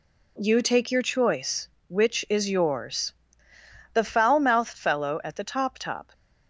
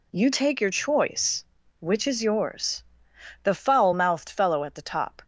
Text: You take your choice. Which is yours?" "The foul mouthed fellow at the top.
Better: second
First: says "top" twice; at 5.7 s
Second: none

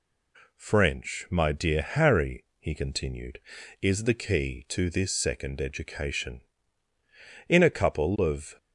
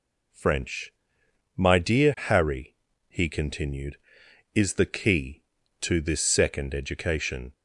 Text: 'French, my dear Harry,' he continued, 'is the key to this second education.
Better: second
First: goes on to say "In a couple of"; noticeable; from 7.4 s on; 1.0 s long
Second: none

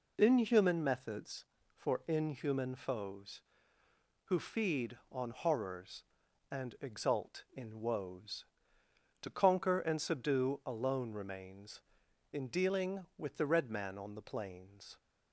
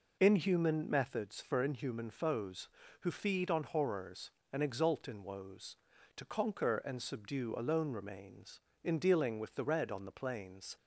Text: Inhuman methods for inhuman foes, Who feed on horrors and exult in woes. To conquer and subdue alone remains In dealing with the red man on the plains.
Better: first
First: none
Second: skips "man"; at 9.8 s

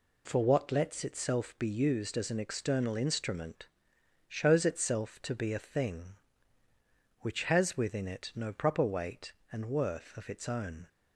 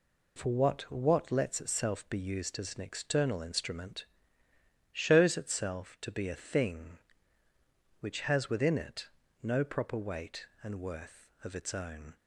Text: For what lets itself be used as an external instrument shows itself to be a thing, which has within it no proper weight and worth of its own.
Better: first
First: pauses between "instrument" and "shows"; noticeable; at 3.6 s; 0.58 s long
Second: says "what" twice; at 0.9 s // pauses between "instrument" and "shows"; noticeable; at 4.0 s; 0.88 s long // pauses between "it" and "no"; slight; at 9.0 s; 0.32 s long

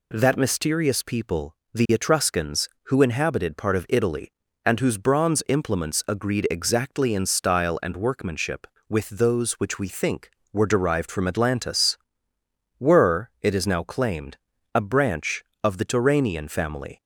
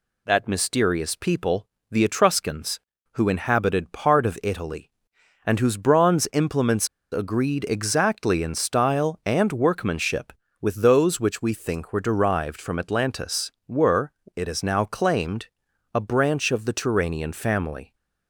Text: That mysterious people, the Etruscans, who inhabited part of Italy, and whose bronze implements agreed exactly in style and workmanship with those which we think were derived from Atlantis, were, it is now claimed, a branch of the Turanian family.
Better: first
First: none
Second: pauses between "implements" and "agreed"; slight; at 6.8 s; 0.25 s long

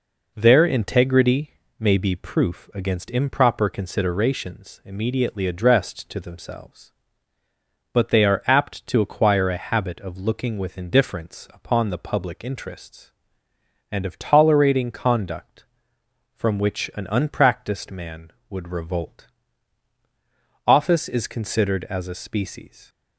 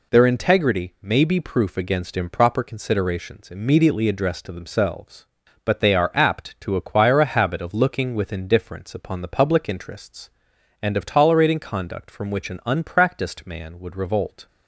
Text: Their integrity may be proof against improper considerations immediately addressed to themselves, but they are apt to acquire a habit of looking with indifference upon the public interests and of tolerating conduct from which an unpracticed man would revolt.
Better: second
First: pauses between "integrity" and "may"; slight; at 1.5 s; 0.28 s long // goes on to say "Office is considered as a species"; strong; from 20.6 s on; 2.2 s long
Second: none

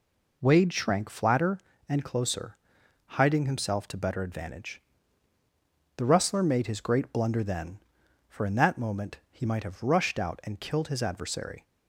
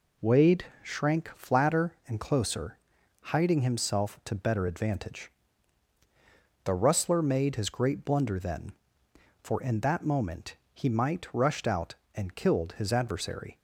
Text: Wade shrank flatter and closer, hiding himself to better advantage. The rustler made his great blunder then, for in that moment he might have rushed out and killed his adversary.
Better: first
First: none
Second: pauses between "Wade" and "shrank"; slight; at 0.6 s; 0.18 s long // pauses between "moment" and "he"; slight; at 10.5 s; 0.18 s long // skips "have"; at 11.3 s

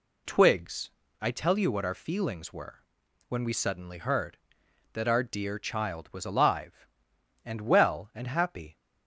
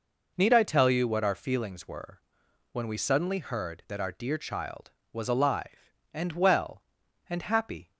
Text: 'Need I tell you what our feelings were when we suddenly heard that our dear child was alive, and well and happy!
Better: second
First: says "Twigs" for "Need"; at 0.2 s // pauses between "were" and "when"; noticeable; at 2.8 s; 0.46 s long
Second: pauses between "were" and "when"; noticeable; at 2.1 s; 0.52 s long

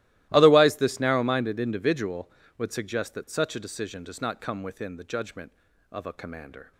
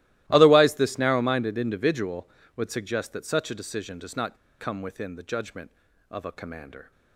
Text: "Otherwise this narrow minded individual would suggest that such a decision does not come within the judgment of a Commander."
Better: first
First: starts louder than the rest; strong; until 1.3 s; 16 dB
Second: starts louder than the rest; strong; until 1.2 s; 16 dB // pauses between "not" and "come"; slight; at 4.3 s; 0.25 s long

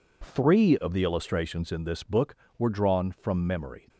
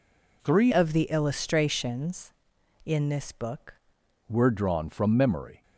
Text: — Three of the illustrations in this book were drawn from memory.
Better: first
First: none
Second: changes voice from "of" to "book"; from 0.7 to 3.7 s; 3.0 s long

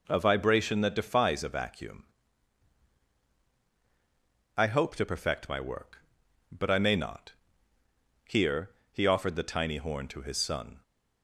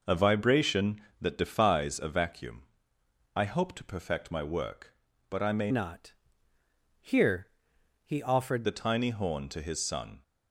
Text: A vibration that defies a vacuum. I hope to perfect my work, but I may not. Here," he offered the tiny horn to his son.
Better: first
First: none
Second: changes voice from "not" to "offered"; from 5.7 to 8.6 s; 2.9 s long

